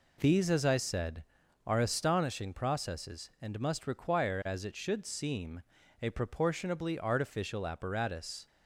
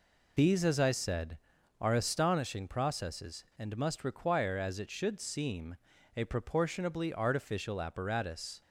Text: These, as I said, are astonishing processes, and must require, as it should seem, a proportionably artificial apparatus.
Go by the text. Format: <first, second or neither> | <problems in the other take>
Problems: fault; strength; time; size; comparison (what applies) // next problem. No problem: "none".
first | loses the start of "These"; at 0.3 s; 45 ms